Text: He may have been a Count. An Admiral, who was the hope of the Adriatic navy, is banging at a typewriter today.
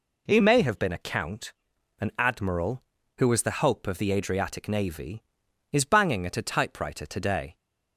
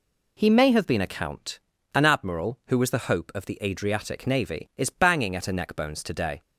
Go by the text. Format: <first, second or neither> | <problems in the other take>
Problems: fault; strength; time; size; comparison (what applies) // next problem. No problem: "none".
first | says "neckbones" for "typewriter"; at 5.5 s